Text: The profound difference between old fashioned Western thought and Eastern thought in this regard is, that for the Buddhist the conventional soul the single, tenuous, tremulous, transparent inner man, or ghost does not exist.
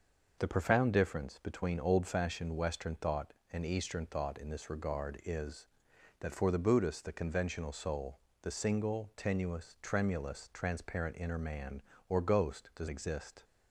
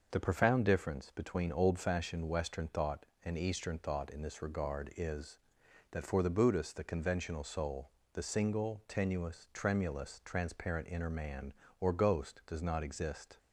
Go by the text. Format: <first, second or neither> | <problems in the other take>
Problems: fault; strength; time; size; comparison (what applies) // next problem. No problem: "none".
second | pauses between "soul" and "the"; slight; at 8.1 s; 0.24 s long; slight in the second // skips "not"; at 12.8 s